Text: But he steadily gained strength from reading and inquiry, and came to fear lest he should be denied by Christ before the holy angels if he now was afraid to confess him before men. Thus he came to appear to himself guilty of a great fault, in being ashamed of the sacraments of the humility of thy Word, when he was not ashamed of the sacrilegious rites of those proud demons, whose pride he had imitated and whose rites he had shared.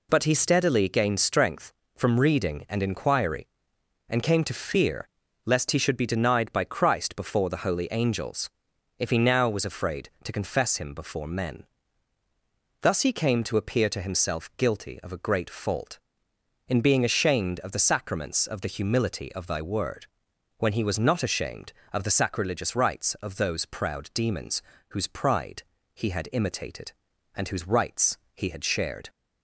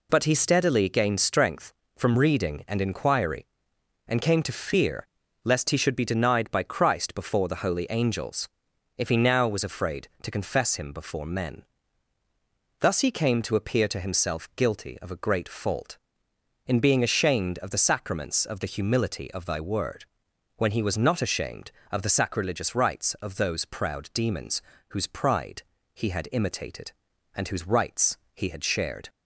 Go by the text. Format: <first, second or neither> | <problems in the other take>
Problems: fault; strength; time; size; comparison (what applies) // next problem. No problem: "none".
neither | pauses between "fear" and "lest"; the same in both // pauses between "angels" and "if"; noticeable; the same in both // pauses between "pride" and "he"; slight; the same in both // pauses between "rites" and "he"; slight; the same in both